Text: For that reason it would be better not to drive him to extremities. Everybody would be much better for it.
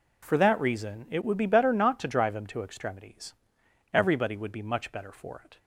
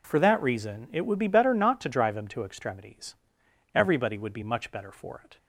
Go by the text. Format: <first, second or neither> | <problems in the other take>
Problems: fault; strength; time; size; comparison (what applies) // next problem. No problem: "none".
neither | none